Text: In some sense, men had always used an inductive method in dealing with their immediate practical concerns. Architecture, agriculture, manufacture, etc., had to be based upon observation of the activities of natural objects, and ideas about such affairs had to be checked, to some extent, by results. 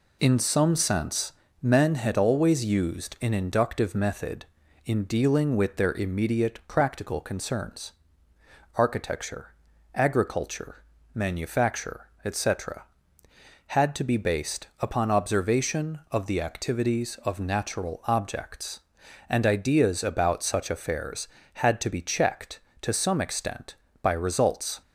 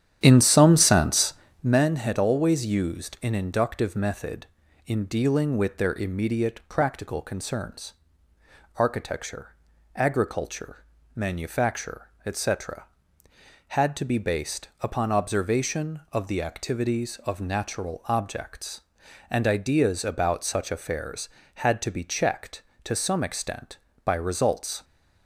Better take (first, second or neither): first